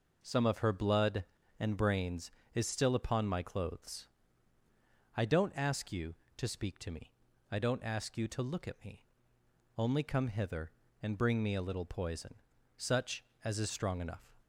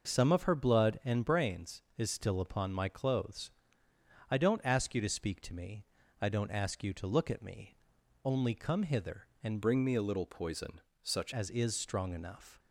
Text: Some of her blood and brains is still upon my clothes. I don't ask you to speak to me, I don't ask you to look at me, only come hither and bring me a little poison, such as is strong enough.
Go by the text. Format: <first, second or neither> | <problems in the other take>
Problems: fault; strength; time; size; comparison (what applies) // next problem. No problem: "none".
first | changes voice from "bring" to "such"; from 9.6 to 11.3 s; 1.7 s long